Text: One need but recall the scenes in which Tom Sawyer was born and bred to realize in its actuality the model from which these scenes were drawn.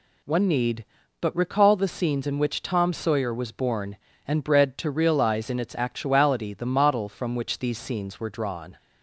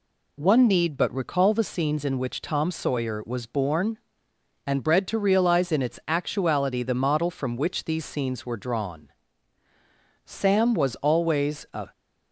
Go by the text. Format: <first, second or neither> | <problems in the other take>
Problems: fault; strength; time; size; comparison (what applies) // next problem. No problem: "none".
first | goes on to say "Sam was always a"; from 10.3 s on; 1.5 s long